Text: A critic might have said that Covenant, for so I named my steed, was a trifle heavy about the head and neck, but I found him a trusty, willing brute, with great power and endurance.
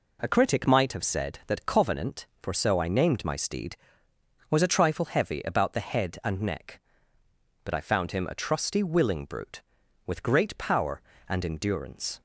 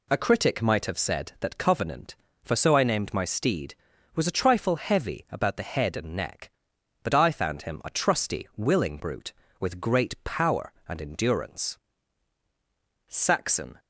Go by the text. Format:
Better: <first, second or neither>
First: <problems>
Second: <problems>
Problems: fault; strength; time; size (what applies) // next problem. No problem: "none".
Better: first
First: none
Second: goes on to say "Saxon"; noticeable; from 13.0 s on; 0.72 s long